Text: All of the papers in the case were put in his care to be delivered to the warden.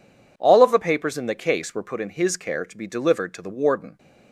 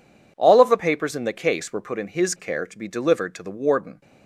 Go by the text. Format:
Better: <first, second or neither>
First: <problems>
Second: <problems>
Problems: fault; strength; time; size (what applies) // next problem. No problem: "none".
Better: neither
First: none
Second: none